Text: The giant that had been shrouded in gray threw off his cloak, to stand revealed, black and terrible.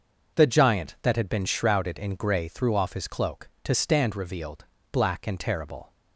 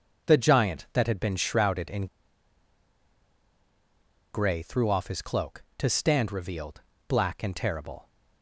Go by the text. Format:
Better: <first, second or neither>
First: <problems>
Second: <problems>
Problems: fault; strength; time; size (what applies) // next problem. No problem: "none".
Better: first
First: none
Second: pauses between "in" and "gray"; strong; at 2.0 s; 2.2 s long